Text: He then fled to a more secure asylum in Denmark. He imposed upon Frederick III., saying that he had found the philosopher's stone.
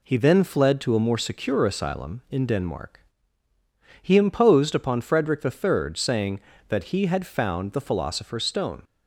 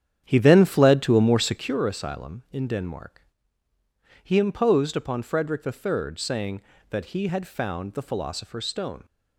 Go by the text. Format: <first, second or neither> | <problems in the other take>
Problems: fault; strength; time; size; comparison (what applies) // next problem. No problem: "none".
first | starts louder than the rest; strong; until 1.8 s; 9 dB